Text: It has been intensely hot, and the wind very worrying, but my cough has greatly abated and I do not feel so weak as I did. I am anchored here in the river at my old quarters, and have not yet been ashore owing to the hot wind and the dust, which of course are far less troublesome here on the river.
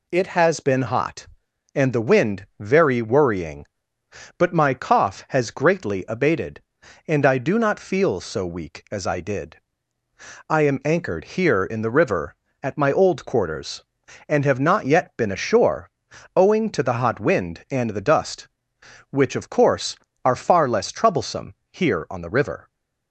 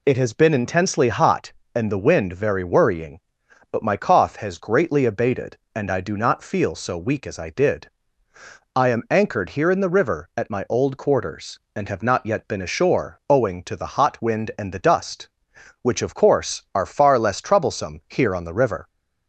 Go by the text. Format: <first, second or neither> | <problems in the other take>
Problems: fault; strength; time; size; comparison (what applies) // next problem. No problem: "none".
second | skips "intensely"; at 0.8 s // pauses between "ashore" and "owing"; noticeable; at 15.8 s; 0.48 s long // pauses between "troublesome" and "here"; slight; at 21.5 s; 0.18 s long